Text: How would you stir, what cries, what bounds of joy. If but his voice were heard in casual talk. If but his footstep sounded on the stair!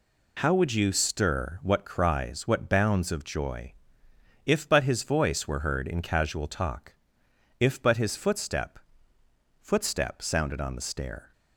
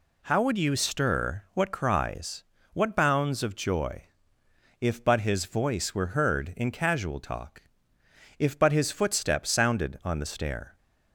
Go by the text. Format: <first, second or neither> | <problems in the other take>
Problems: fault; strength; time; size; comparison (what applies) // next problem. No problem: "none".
second | says "footstep" twice; at 9.5 s